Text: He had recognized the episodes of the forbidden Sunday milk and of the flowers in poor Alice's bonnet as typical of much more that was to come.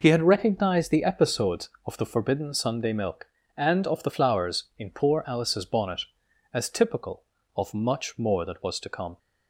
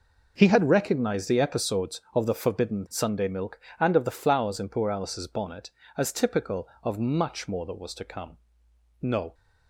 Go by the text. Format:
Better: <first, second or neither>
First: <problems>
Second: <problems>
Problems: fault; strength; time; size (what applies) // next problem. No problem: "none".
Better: first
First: none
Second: goes on to say "No"; slight; from 9.0 s on; 0.32 s long